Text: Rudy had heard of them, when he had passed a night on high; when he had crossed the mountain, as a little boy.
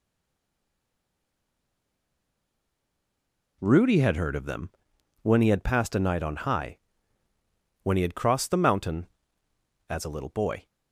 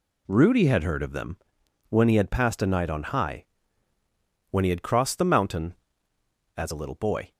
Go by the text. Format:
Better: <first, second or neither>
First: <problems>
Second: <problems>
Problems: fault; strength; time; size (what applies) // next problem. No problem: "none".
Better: second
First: stays silent before the first word; strong; until 3.6 s; 3.6 s long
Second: none